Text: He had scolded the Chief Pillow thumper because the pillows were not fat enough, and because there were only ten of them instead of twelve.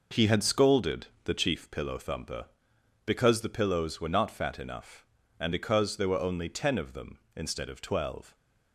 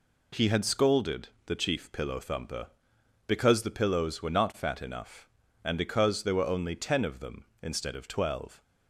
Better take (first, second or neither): second